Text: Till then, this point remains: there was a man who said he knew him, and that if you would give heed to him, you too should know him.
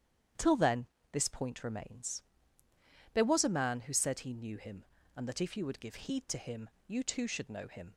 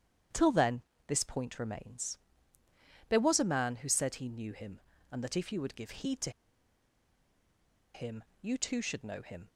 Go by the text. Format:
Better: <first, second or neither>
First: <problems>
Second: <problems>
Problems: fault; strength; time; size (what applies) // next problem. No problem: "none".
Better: first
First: starts louder than the rest; strong; until 1.6 s; 9.5 dB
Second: starts louder than the rest; strong; until 1.5 s; 9.5 dB // pauses between "to" and "him"; strong; at 6.2 s; 1.6 s long